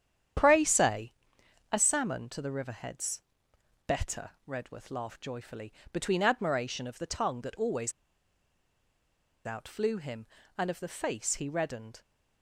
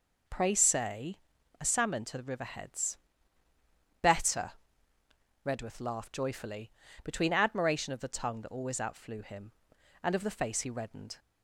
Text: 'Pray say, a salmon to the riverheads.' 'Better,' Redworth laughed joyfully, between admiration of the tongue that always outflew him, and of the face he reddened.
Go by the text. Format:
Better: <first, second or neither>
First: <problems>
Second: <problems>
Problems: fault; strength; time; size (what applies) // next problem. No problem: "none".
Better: second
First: starts louder than the rest; strong; until 1.9 s; 9.5 dB // pauses between "always" and "outflew"; strong; at 7.9 s; 1.5 s long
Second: none